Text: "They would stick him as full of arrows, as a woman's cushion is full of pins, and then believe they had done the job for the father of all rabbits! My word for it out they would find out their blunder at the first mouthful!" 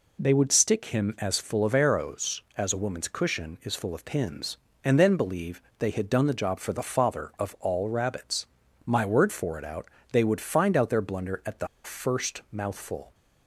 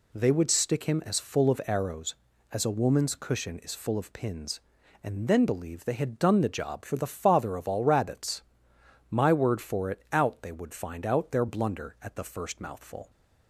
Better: second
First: pauses between "believe" and "they"; slight; at 5.6 s; 0.16 s long // pauses between "out" and "they"; slight; at 9.8 s; 0.24 s long // pauses between "the" and "first"; slight; at 11.6 s; 0.18 s long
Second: none

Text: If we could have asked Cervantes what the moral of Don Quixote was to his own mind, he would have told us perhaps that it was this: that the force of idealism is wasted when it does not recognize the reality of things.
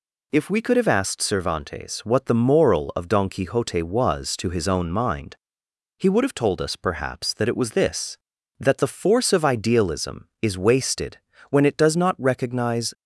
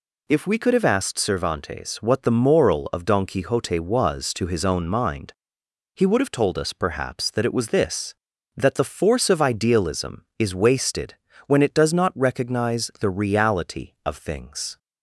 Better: second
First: pauses between "wasted" and "when"; slight; at 11.1 s; 0.32 s long // stops before "the reality of things"; at 12.9 s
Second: pauses between "wasted" and "when"; slight; at 11.1 s; 0.32 s long

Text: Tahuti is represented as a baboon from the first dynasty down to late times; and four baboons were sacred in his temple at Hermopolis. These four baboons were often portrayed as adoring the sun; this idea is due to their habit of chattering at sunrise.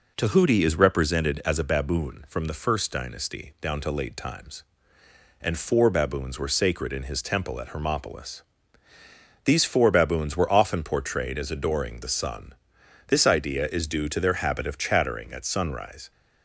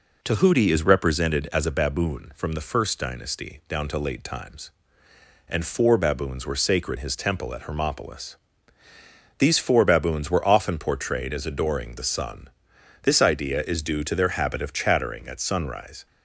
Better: first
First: none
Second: skips "in"; at 6.9 s

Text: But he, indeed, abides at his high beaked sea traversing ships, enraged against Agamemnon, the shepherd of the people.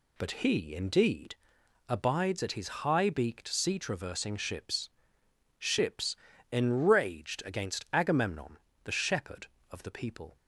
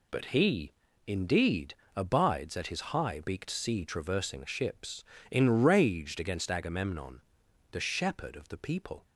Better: second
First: says "ships" twice; at 5.5 s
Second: none

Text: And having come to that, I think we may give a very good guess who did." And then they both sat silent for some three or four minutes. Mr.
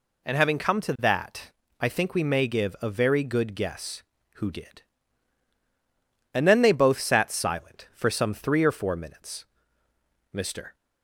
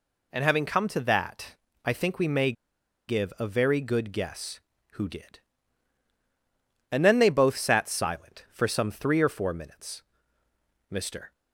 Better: first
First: none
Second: pauses between "may" and "give"; noticeable; at 2.5 s; 0.55 s long

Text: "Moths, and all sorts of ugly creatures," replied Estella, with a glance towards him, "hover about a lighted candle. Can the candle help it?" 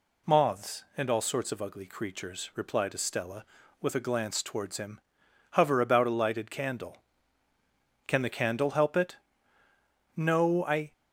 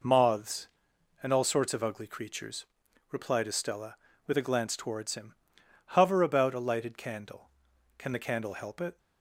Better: second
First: goes on to say "No I"; noticeable; from 10.1 s on; 0.76 s long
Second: none

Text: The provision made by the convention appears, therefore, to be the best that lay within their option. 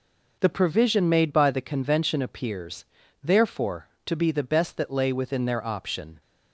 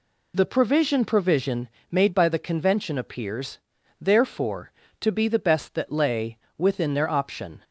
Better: first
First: none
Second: says "provision" twice; at 1.0 s // pauses between "lay" and "within"; slight; at 6.3 s; 0.20 s long

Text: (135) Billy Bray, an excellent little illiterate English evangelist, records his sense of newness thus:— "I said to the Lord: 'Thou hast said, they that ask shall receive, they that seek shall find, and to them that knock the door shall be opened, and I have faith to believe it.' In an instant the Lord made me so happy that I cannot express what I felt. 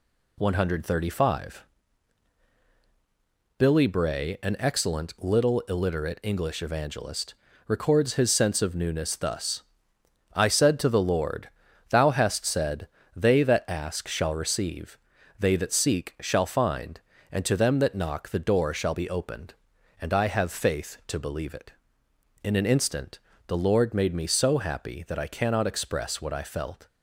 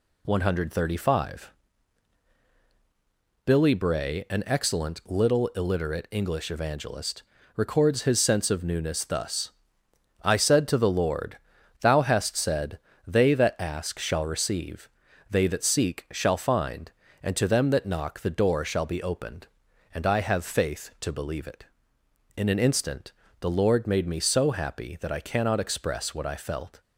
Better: neither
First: pauses between "instant" and "the"; slight; at 23.1 s; 0.28 s long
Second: pauses between "instant" and "the"; slight; at 23.1 s; 0.28 s long

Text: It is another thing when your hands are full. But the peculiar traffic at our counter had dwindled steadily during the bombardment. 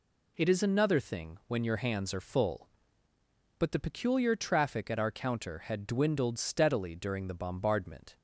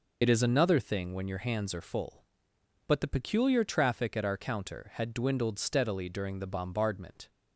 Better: first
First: none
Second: loses the start of "It"; at 0.2 s; 50 ms

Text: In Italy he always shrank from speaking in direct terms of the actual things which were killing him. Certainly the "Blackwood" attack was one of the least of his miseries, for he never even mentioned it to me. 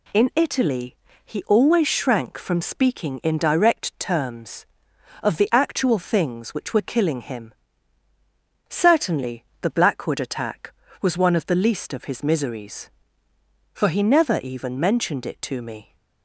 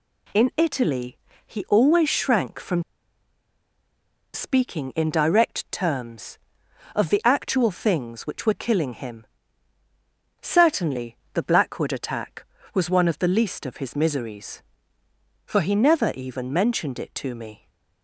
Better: first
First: pauses between "Italy" and "he"; slight; at 0.9 s; 0.28 s long // pauses between "Certainly" and "the"; slight; at 9.4 s; 0.18 s long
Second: pauses between "Italy" and "he"; slight; at 1.1 s; 0.28 s long // pauses between "from" and "speaking"; strong; at 2.8 s; 1.5 s long // pauses between "Certainly" and "the"; slight; at 11.1 s; 0.18 s long

